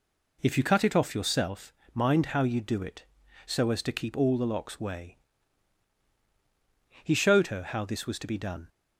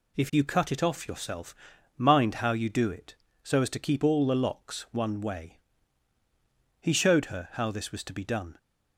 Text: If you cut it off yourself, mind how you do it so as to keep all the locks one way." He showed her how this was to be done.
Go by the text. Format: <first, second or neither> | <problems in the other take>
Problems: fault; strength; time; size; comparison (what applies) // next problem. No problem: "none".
second | skips "one"; at 4.7 s